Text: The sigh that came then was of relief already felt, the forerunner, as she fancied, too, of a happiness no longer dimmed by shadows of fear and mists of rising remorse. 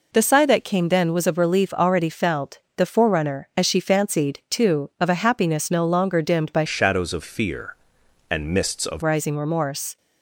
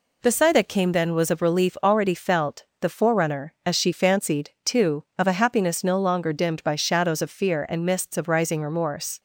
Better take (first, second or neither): second